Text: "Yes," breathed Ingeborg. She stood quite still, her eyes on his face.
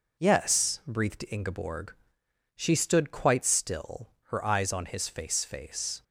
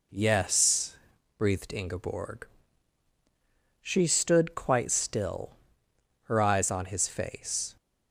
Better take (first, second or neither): second